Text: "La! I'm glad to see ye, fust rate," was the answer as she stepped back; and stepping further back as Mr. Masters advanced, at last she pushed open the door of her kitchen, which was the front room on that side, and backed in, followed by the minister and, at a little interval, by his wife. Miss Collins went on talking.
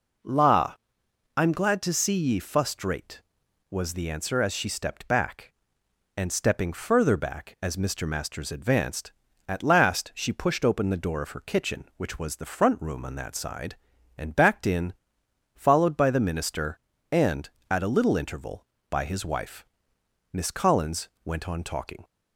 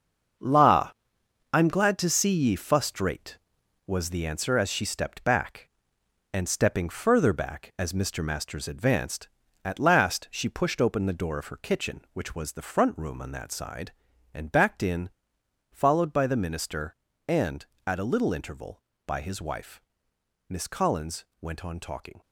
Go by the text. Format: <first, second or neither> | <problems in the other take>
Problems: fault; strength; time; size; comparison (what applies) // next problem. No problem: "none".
first | gets quieter; strong; throughout; 9 dB // pauses between "Collins" and "went"; slight; at 21.2 s; 0.16 s long; slight in the first